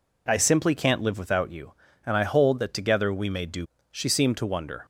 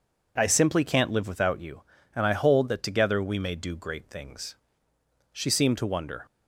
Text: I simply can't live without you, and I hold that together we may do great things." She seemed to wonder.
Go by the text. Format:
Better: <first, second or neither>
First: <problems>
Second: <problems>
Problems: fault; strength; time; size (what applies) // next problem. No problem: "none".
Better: second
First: skips "great things"; at 3.7 s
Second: none